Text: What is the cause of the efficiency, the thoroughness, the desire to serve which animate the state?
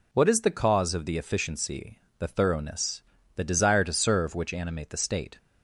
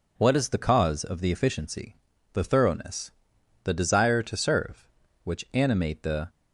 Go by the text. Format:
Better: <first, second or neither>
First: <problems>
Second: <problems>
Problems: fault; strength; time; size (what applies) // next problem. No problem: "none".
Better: first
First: none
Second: stops before "state"; at 6.2 s